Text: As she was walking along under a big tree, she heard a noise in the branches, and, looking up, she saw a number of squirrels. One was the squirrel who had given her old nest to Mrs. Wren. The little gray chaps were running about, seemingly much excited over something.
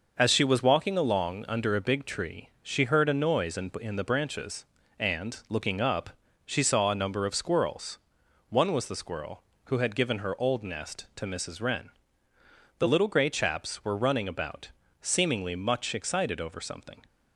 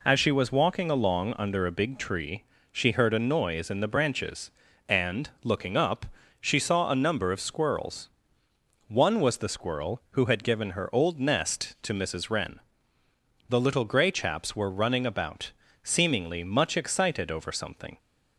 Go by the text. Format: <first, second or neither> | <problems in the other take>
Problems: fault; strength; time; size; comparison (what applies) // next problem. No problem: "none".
second | says "in" twice; at 3.7 s